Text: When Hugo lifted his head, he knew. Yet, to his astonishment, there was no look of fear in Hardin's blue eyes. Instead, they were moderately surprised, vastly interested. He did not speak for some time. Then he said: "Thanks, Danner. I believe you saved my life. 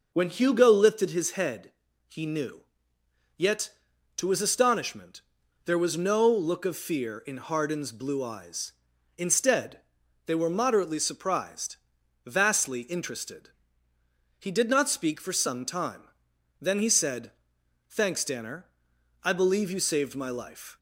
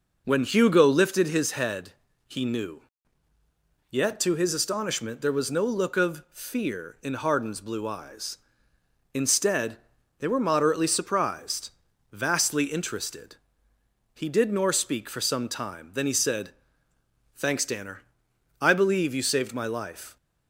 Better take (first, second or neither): first